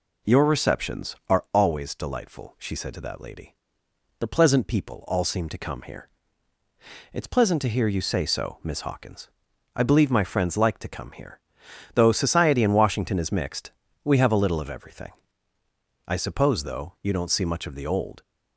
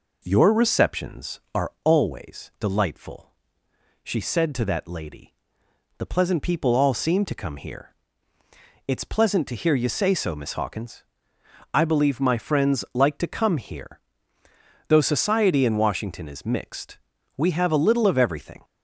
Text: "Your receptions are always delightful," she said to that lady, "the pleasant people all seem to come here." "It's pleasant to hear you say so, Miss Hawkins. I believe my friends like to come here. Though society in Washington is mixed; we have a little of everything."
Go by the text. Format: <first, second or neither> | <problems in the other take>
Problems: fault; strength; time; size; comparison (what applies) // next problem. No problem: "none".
second | goes on to say "I suppose though you don't see much of the old"; strong; from 16.0 s on; 2.1 s long